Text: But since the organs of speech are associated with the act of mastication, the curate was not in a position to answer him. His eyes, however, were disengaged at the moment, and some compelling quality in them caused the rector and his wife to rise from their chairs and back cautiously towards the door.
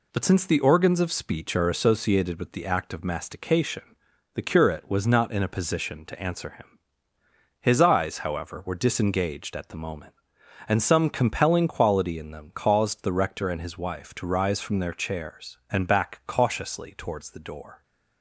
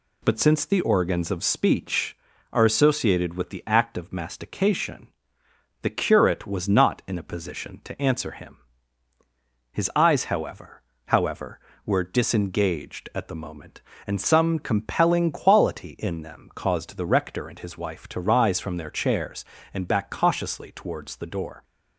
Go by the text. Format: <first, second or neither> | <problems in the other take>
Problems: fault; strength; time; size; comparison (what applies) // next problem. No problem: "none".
first | says "however" twice; at 11.0 s